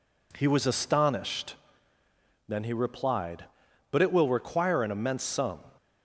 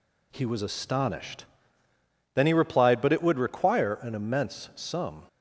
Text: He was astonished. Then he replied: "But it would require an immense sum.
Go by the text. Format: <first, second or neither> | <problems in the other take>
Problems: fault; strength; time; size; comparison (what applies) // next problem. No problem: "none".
second | says "will" for "would"; at 4.1 s